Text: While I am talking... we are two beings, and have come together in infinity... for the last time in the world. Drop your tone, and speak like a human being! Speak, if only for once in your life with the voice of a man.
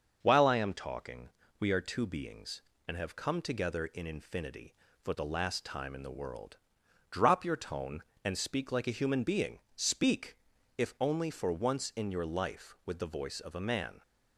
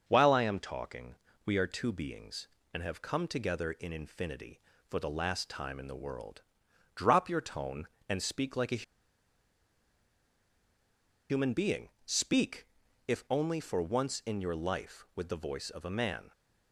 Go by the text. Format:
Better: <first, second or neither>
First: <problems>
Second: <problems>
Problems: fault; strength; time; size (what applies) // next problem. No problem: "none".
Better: first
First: starts louder than the rest; until 1.2 s; 6.5 dB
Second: starts louder than the rest; until 1.0 s; 6.5 dB // pauses between "a" and "human"; strong; at 8.8 s; 2.4 s long